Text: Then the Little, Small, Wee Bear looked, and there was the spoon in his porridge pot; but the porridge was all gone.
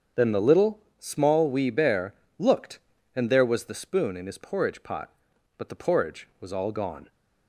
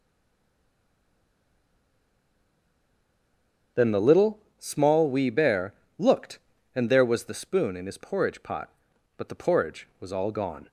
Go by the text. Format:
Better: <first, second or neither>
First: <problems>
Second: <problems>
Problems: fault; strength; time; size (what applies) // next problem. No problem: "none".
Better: first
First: starts louder than the rest; until 1.3 s; 7 dB // pauses between "Bear" and "looked"; slight; at 2.1 s; 0.24 s long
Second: stays silent before the first word; strong; until 3.7 s; 3.7 s long // starts louder than the rest; until 4.9 s; 7 dB // pauses between "Bear" and "looked"; slight; at 5.7 s; 0.24 s long